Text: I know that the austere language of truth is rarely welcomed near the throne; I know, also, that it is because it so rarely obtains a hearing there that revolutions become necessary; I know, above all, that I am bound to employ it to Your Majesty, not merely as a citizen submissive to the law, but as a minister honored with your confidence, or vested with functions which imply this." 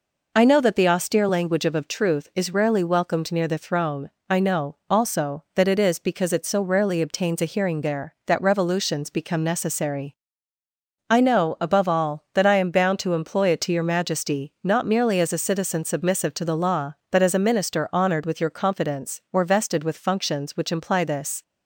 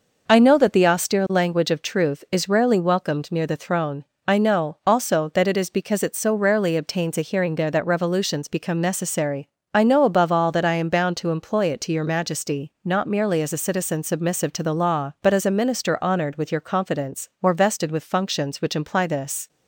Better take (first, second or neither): second